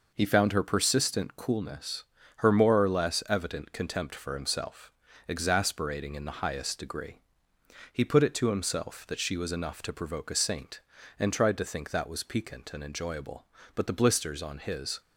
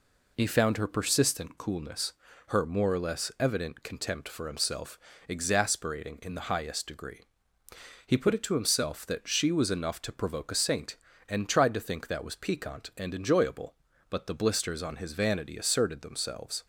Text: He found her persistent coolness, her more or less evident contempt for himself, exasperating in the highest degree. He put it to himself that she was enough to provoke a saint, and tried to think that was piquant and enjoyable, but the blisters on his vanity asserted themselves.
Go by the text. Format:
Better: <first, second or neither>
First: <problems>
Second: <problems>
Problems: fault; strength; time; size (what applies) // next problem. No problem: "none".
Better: second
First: stops before "vanity asserted themselves"; at 15.0 s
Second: none